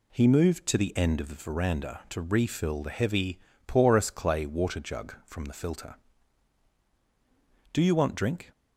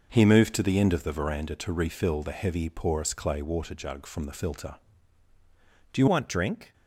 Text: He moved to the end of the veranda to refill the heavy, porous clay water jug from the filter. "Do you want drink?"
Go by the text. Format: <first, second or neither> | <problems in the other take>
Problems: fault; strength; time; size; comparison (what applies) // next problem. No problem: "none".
first | changes voice at "want"; from 6.0 s on; 0.7 s long